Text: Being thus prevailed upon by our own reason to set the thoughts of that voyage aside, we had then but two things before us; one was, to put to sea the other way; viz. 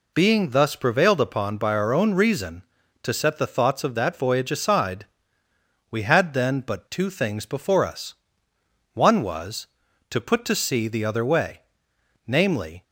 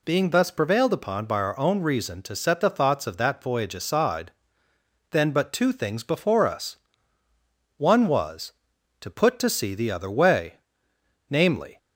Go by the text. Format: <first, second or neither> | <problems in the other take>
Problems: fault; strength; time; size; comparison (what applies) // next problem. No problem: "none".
first | skips "we had"; at 4.7 s